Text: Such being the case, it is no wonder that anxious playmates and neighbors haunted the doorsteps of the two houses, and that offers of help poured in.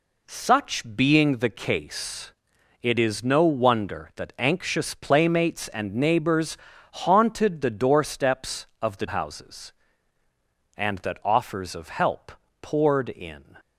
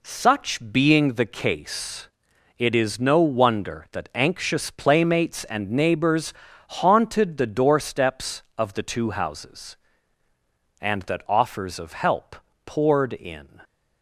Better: second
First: pauses between "neighbors" and "haunted"; slight; at 6.5 s; 0.36 s long // skips "two"; at 9.0 s // pauses between "help" and "poured"; slight; at 12.3 s; 0.28 s long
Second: pauses between "neighbors" and "haunted"; slight; at 6.3 s; 0.36 s long // pauses between "help" and "poured"; slight; at 12.3 s; 0.28 s long

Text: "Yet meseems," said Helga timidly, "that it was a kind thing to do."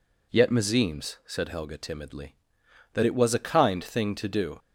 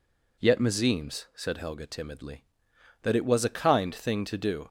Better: neither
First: none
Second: none

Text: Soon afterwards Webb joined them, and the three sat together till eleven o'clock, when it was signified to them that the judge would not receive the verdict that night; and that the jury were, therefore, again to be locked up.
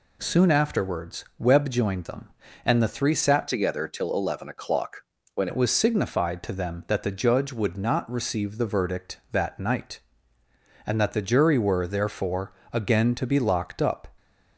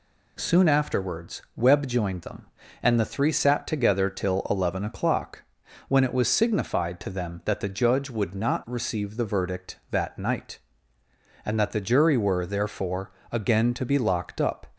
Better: second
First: changes voice from "together" to "when"; from 3.4 to 5.4 s; 2.0 s long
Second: none

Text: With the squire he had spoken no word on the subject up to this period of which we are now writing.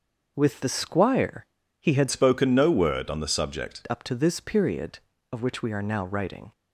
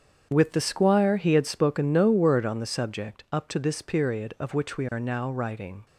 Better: second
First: starts louder than the rest; until 1.3 s; 6 dB // pauses between "squire" and "he"; slight; at 1.4 s; 0.34 s long // changes voice from "spoken" to "subject"; from 2.0 to 3.8 s; 1.8 s long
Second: starts louder than the rest; strong; until 1.3 s; 7.5 dB

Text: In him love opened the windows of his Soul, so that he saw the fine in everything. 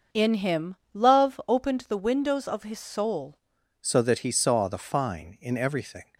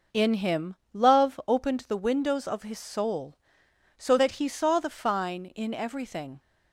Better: second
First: pauses between "him" and "love"; slight; at 0.7 s; 0.18 s long // changes voice at "so"; from 3.8 s on; 2.2 s long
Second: pauses between "him" and "love"; slight; at 0.7 s; 0.18 s long

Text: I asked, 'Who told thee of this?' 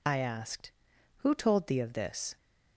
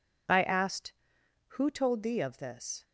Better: neither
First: none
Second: none

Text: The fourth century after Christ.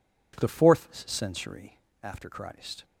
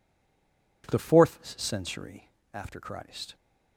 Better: first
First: pauses between "fourth" and "century"; slight; at 0.8 s; 0.18 s long // pauses between "century" and "after"; slight; at 1.7 s; 0.24 s long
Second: stays silent before the first word; slight; until 0.8 s; 0.8 s long // pauses between "fourth" and "century"; slight; at 1.3 s; 0.18 s long // pauses between "century" and "after"; slight; at 2.2 s; 0.24 s long

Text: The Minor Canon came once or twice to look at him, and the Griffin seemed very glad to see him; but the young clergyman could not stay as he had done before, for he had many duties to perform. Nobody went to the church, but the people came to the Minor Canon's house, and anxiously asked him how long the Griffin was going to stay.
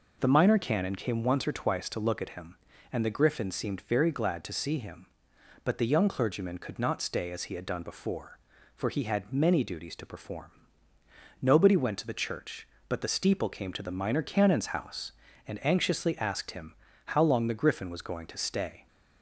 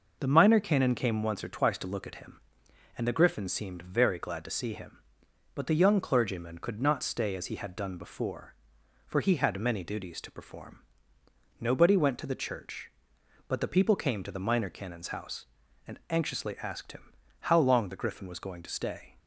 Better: second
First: says "steeple" for "people"; at 13.0 s // pauses between "him" and "how"; slight; at 16.7 s; 0.30 s long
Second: pauses between "him" and "how"; slight; at 17.1 s; 0.28 s long

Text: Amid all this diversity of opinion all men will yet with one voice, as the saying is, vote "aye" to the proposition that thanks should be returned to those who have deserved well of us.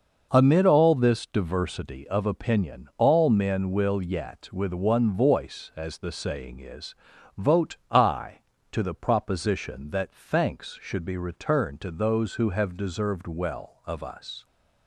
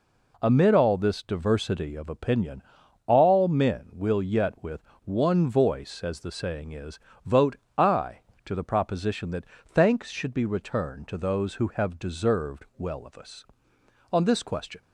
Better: first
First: none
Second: pauses between "opinion" and "all"; at 2.6 s; 0.44 s long // pauses between "with" and "one"; slight; at 4.8 s; 0.22 s long // pauses between "vote" and "aye"; slight; at 7.5 s; 0.22 s long // pauses between "that" and "thanks"; slight; at 9.4 s; 0.22 s long // goes on to say "On this question"; noticeable; from 14.1 s on; 0.70 s long

